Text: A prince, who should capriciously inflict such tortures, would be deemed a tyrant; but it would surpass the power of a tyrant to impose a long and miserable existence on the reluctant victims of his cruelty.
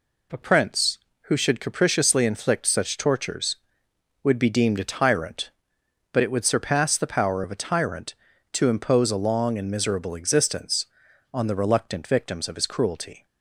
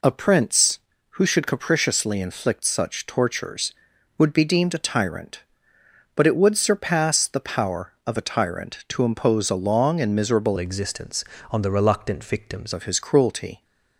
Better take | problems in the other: first | changes voice from "existence" to "victims"; from 10.5 to 12.7 s; 2.2 s long

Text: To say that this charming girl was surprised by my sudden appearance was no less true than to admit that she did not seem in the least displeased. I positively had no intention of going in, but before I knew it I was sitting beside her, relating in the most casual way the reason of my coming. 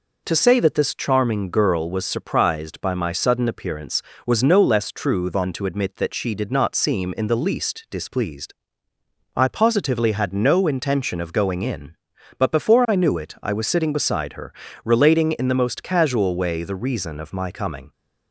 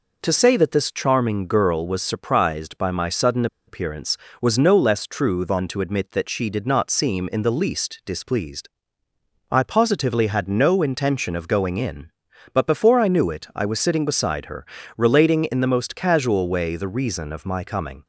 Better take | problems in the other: first | pauses between "sudden" and "appearance"; slight; at 3.4 s; 0.21 s long

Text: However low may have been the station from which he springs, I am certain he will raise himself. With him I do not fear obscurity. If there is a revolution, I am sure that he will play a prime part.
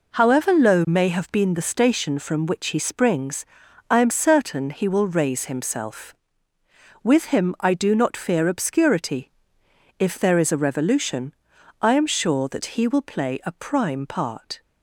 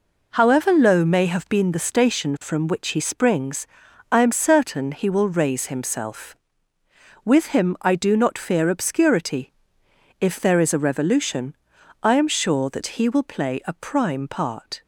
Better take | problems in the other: neither | none

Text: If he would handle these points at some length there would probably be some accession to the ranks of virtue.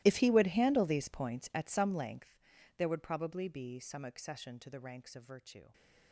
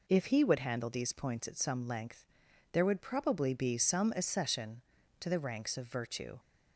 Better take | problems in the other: second | gets quieter; strong; throughout; 20 dB // pauses between "length" and "there"; at 2.3 s; 0.40 s long; noticeable in the second

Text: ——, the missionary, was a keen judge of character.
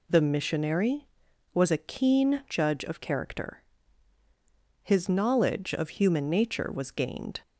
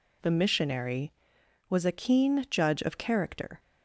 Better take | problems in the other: second | goes on to say "His knowledge of human nature was gained"; strong; from 4.8 s on; 2.5 s long

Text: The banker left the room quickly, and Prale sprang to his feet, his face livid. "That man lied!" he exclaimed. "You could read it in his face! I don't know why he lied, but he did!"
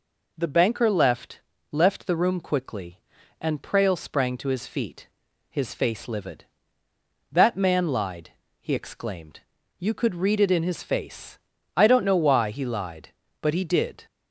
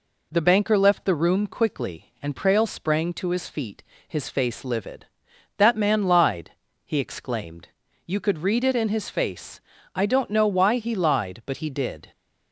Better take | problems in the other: second | says "left" twice; at 1.7 s

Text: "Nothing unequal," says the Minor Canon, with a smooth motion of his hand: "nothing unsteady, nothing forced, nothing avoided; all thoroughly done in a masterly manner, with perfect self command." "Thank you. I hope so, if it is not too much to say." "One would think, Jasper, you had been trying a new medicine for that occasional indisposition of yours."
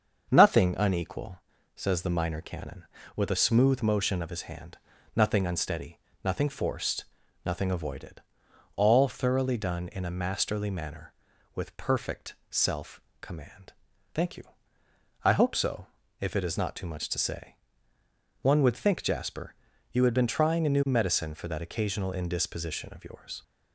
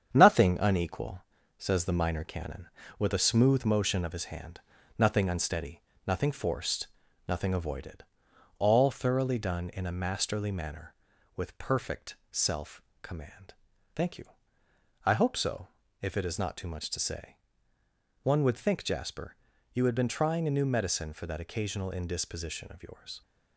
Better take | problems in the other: first | gets quieter; noticeable; throughout; 4 dB // starts louder than the rest; strong; until 1.1 s; 8 dB; also in the first // pauses between "perfect" and "self"; slight; at 12.1 s; 0.16 s long; slight in the first // pauses between "self" and "command"; slight; at 12.8 s; 0.22 s long; slight in the first

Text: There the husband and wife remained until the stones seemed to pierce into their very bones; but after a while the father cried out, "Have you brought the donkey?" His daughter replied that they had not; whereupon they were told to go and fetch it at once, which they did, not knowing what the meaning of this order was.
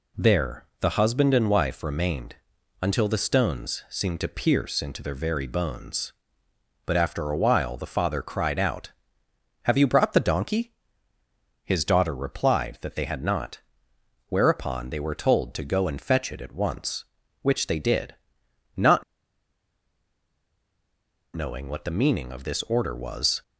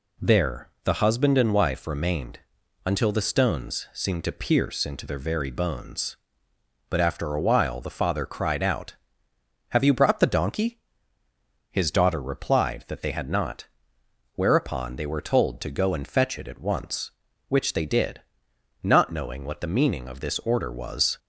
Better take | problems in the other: second | pauses between "remained" and "until"; noticeable; at 2.3 s; 0.46 s long; noticeable in the second // pauses between "not" and "knowing"; strong; at 19.0 s; 2.3 s long

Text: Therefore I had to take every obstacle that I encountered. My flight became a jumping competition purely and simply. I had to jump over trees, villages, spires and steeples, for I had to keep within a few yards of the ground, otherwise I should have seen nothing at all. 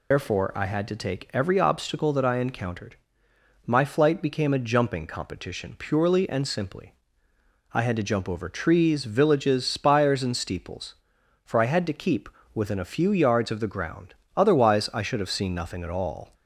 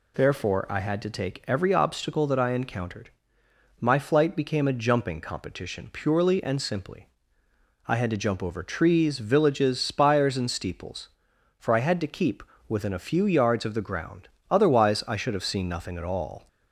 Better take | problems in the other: second | loses the start of "Therefore"; at 0.1 s; 95 ms // pauses between "keep" and "within"; slight; at 12.2 s; 0.26 s long; slight in the second

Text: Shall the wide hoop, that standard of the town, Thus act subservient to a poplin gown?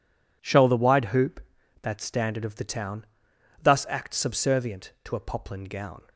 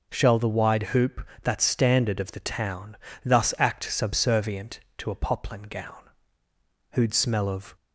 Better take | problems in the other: first | goes on to say "Who'd smell of"; noticeable; from 6.9 s on; 0.84 s long

